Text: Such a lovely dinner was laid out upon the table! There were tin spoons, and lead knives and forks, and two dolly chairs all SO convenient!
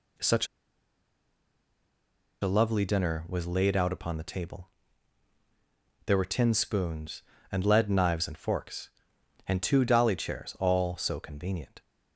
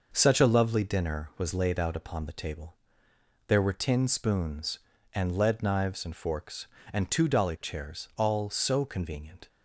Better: second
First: pauses between "Such" and "a"; strong; at 0.4 s; 1.9 s long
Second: none

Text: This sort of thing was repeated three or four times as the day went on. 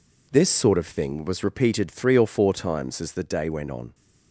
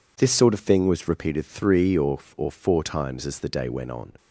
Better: first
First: none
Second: says "or" twice; at 2.3 s

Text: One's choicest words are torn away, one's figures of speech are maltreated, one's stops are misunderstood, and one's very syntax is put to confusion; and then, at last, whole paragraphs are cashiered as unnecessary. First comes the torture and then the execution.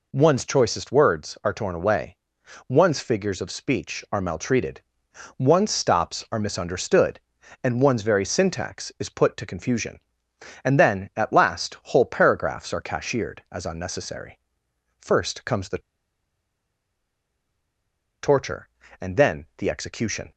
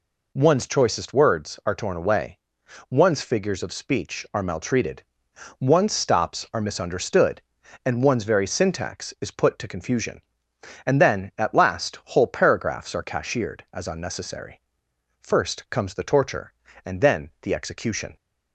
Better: second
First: pauses between "the" and "torture"; strong; at 15.8 s; 2.4 s long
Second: none

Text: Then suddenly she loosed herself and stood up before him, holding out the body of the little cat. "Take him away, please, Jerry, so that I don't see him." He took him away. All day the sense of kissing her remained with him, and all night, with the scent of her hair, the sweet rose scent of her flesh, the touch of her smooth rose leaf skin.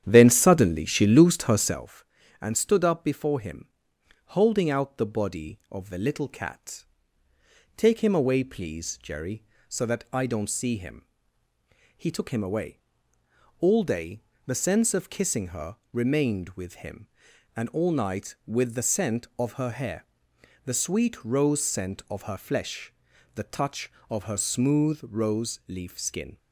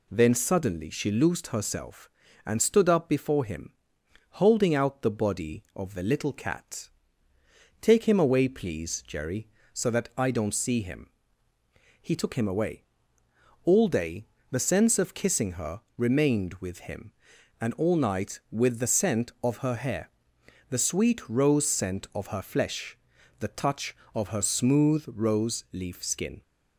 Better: second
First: starts louder than the rest; strong; until 1.9 s; 9.5 dB // pauses between "day" and "the"; slight; at 14.2 s; 0.24 s long // pauses between "her" and "remained"; slight; at 15.7 s; 0.16 s long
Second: pauses between "day" and "the"; slight; at 14.2 s; 0.24 s long // pauses between "her" and "remained"; slight; at 15.8 s; 0.16 s long

